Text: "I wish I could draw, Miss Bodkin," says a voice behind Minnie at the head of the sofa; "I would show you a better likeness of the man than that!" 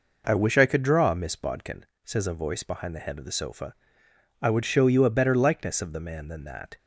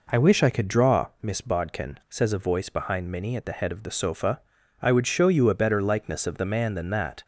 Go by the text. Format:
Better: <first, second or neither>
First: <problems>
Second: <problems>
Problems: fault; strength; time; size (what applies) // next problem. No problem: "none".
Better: second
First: skips "Minnie at"; at 2.9 s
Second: none